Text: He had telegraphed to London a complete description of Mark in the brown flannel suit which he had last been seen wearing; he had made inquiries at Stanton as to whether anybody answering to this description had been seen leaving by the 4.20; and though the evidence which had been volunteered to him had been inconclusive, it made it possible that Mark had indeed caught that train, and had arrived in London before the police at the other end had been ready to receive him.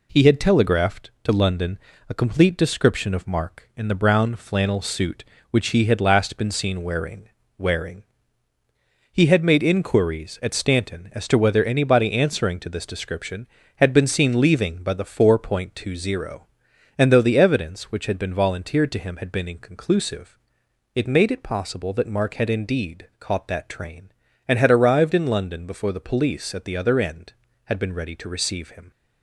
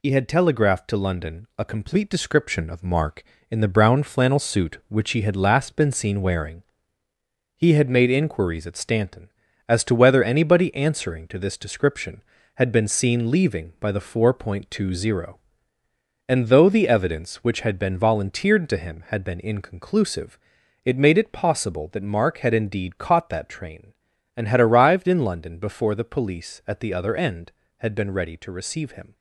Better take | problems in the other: second | pauses between "London" and "a"; slight; at 1.7 s; 0.30 s long // says "wearing" twice; at 7.5 s

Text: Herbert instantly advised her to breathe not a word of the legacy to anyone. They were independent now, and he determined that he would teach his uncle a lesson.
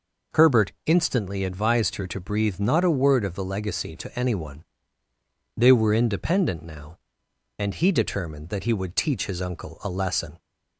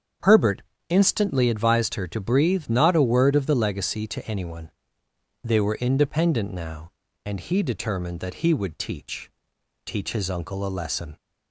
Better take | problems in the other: first | starts louder than the rest; strong; until 1.5 s; 8 dB // pauses between "Herbert" and "instantly"; slight; at 0.6 s; 0.30 s long; slight in the first // says "teach" twice; at 9.8 s

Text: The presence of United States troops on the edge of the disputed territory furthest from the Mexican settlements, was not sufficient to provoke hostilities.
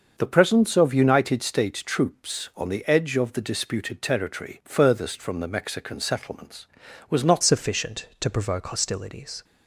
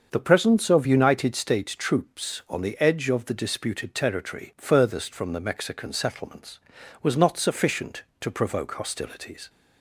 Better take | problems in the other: second | starts louder than the rest; until 1.1 s; 6.5 dB; also in the second // changes voice at "sufficient"; from 7.4 s on; 2.0 s long

